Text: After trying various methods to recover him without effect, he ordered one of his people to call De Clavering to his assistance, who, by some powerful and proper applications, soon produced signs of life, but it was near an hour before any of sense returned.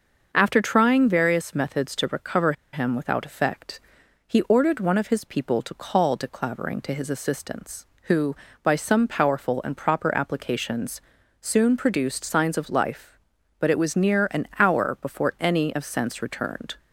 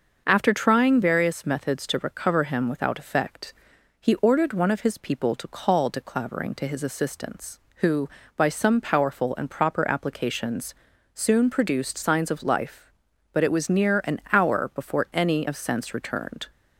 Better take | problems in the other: second | starts louder than the rest; until 1.3 s; 6 dB; also in the second // pauses between "recover" and "him"; slight; at 2.5 s; 0.19 s long

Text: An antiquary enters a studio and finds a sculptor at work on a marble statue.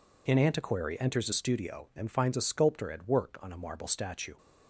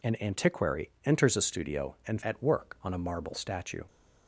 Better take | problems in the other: first | skips "finds a sculptor"; at 2.2 s

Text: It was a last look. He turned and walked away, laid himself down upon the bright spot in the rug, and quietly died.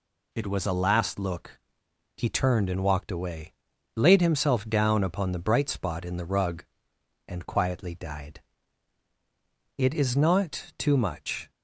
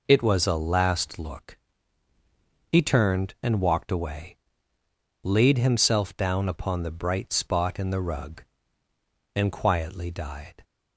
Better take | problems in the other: second | goes on to say "It is not too much"; strong; from 9.7 s on; 1.7 s long

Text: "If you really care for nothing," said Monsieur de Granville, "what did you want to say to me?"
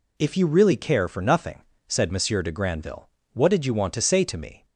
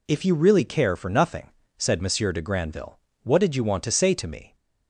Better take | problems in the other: neither | none

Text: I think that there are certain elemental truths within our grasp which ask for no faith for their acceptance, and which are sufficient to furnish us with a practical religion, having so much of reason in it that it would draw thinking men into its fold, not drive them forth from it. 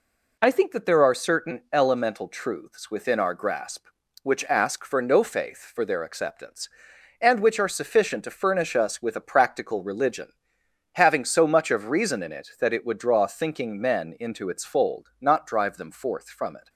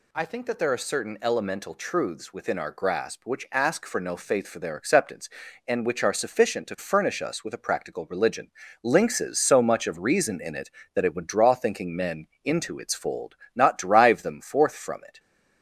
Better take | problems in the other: first | says "lynxes" for "having"; at 8.8 s // pauses between "men" and "into"; slight; at 12.2 s; 0.18 s long

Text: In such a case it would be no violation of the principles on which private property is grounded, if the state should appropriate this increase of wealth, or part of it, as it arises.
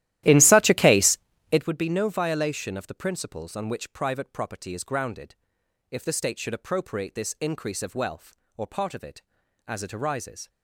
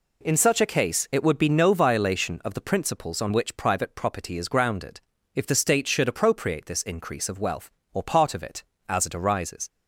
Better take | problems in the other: second | starts louder than the rest; strong; until 1.7 s; 14 dB // pauses between "case" and "it"; slight; at 1.1 s; 0.32 s long

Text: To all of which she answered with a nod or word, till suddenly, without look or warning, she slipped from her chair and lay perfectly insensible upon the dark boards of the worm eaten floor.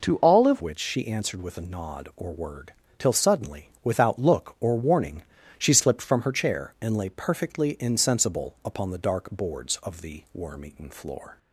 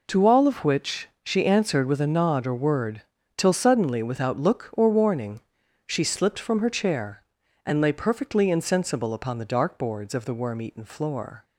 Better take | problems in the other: second | changes voice at "which"; from 0.6 s on; 10.7 s long

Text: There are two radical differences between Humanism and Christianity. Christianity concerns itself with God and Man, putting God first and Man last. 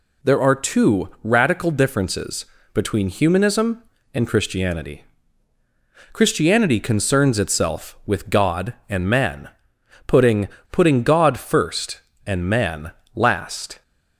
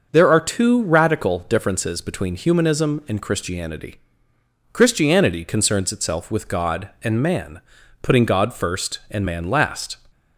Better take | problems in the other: second | pauses between "differences" and "between"; slight; at 2.4 s; 0.28 s long // says "putting" twice; at 10.6 s // pauses between "Man" and "last"; slight; at 12.9 s; 0.24 s long

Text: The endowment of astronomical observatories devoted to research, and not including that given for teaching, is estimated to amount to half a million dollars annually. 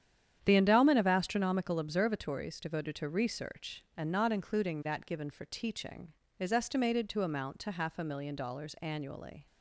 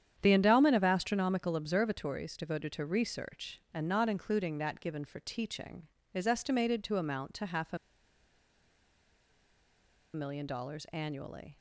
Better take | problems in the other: first | starts louder than the rest; strong; until 1.2 s; 9 dB; strong in the first // pauses between "a" and "million"; strong; at 7.7 s; 2.3 s long

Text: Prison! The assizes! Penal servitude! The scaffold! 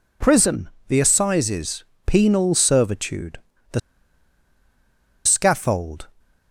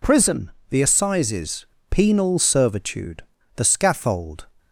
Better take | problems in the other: second | pauses between "The" and "scaffold"; strong; at 3.7 s; 1.4 s long

